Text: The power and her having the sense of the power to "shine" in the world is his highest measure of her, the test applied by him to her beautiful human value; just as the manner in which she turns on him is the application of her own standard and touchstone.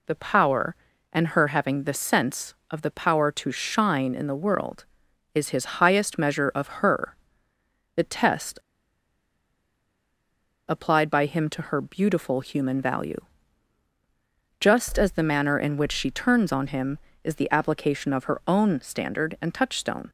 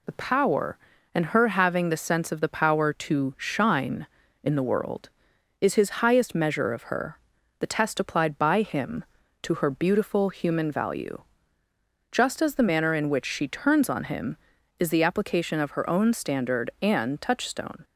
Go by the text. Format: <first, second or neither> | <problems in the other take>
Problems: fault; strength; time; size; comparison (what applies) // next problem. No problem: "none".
second | pauses between "test" and "applied"; strong; at 8.5 s; 2.0 s long